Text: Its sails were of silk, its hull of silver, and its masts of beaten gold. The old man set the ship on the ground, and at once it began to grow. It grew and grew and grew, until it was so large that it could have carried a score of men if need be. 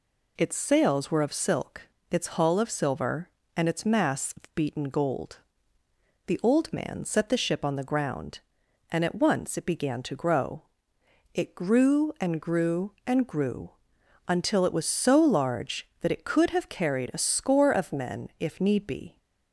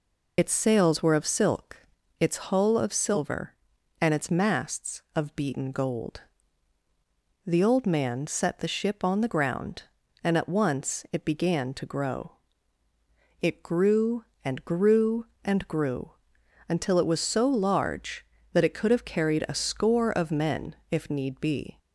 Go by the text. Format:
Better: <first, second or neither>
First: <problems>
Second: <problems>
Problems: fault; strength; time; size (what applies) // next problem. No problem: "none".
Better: first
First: none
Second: loses the start of "Its"; at 0.3 s; 60 ms